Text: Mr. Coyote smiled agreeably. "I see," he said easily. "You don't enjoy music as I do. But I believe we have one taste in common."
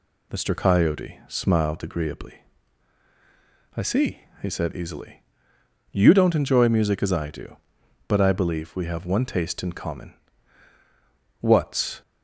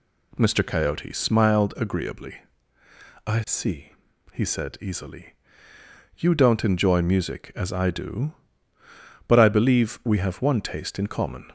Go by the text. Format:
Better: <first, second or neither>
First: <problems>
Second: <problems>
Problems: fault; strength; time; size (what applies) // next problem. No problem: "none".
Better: second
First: goes on to say "What's"; from 11.4 s on; 0.60 s long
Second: none